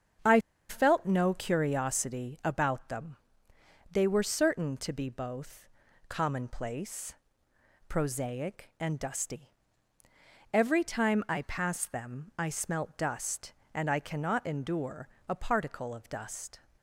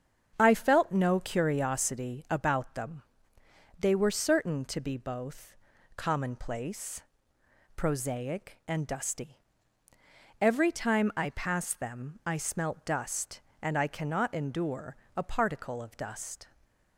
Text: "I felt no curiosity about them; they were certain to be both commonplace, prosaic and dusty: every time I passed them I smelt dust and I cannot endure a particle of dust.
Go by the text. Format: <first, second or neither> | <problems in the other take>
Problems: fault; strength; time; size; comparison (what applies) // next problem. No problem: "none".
second | starts louder than the rest; strong; until 1.5 s; 7.5 dB; strong in the second // pauses between "I" and "felt"; slight; at 0.3 s; 0.31 s long // pauses between "both" and "commonplace"; at 5.6 s; 0.40 s long; also in the second // pauses between "endure" and "a"; slight; at 15.0 s; 0.22 s long; slight in the second